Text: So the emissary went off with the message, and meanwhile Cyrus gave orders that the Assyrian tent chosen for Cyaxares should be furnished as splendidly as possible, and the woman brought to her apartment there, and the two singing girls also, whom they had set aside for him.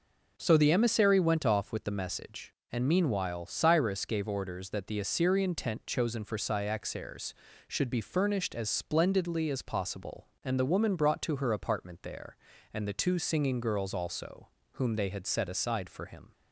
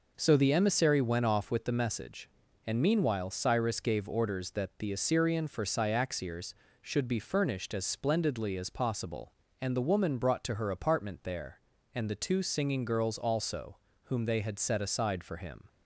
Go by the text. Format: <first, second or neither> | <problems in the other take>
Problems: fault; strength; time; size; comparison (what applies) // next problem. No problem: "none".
first | skips "tent chosen"; at 5.4 s